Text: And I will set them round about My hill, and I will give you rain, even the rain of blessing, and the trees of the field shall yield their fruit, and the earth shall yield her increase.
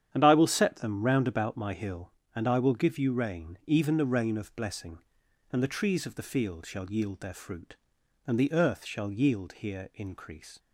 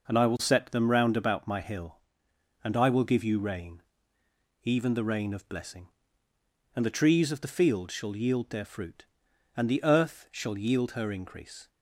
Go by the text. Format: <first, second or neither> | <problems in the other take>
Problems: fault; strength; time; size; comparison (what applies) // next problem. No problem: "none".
second | starts louder than the rest; strong; until 1.1 s; 9.5 dB // says "here" for "her"; at 9.5 s